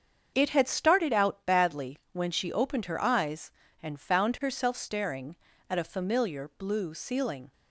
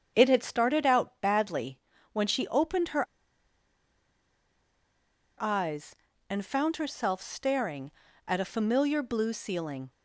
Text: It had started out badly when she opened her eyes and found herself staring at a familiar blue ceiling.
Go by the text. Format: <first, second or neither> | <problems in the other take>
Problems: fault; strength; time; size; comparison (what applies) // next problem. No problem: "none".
first | starts louder than the rest; strong; until 1.1 s; 7.5 dB; also in the first // pauses between "badly" and "when"; slight; at 1.8 s; 0.32 s long // pauses between "her" and "eyes"; strong; at 3.0 s; 2.3 s long